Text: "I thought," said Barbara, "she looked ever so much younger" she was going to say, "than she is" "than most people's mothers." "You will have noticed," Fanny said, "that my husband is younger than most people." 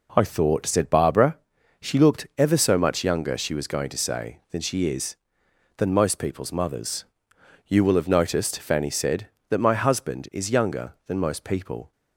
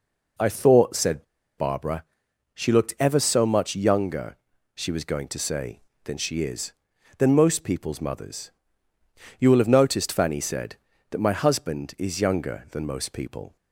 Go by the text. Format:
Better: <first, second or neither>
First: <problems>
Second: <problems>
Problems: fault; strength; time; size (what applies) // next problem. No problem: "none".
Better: first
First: none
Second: pauses between "said" and "Barbara"; slight; at 1.2 s; 0.33 s long // pauses between "younger" and "she"; at 4.3 s; 0.40 s long